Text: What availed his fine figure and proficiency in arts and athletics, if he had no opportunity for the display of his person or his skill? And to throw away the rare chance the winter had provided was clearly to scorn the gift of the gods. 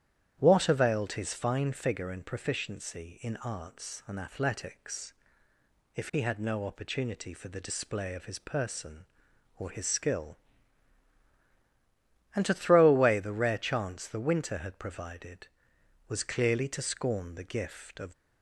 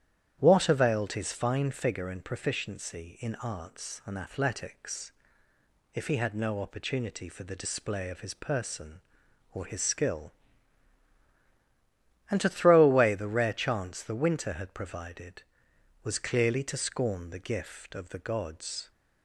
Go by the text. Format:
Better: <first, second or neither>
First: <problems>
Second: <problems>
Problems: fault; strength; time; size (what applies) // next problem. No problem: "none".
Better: second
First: starts louder than the rest; strong; until 1.4 s; 10.5 dB // stops before "the gods"; at 18.1 s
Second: starts louder than the rest; strong; until 1.4 s; 10.5 dB